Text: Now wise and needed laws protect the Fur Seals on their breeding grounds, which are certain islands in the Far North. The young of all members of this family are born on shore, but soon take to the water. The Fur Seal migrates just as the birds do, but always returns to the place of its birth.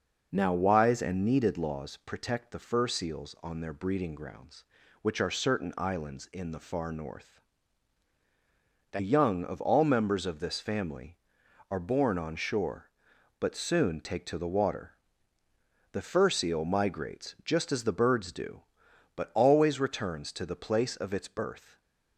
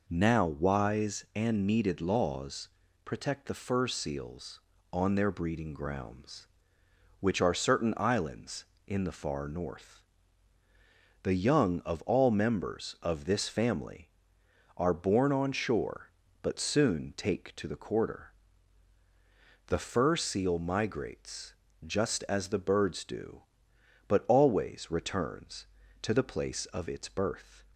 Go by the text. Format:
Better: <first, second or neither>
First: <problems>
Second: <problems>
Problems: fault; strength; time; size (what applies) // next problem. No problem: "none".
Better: first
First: none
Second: pauses between "laws" and "protect"; slight; at 2.6 s; 0.34 s long // says "quarter" for "water"; at 17.7 s // pauses between "migrates" and "just"; slight; at 21.5 s; 0.30 s long